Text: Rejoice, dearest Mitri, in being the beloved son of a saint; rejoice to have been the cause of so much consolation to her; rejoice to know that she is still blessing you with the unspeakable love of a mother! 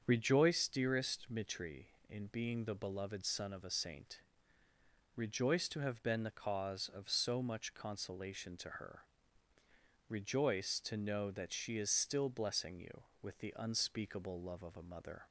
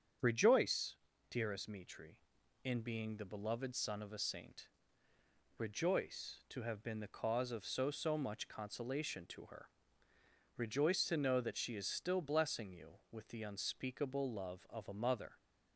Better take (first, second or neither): first